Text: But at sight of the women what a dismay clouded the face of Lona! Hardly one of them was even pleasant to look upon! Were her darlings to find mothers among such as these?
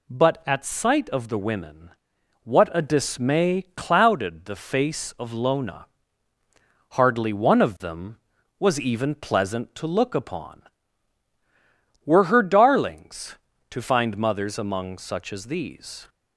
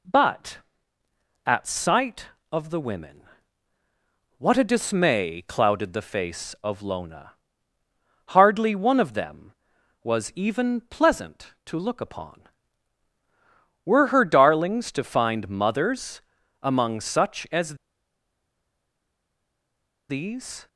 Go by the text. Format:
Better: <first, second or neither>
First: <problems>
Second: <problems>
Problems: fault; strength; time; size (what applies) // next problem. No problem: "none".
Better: first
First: pauses between "women" and "what"; noticeable; at 1.8 s; 0.54 s long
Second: pauses between "women" and "what"; at 3.2 s; 1.1 s long // pauses between "mothers" and "among"; at 16.2 s; 0.40 s long // pauses between "as" and "these"; strong; at 17.7 s; 2.3 s long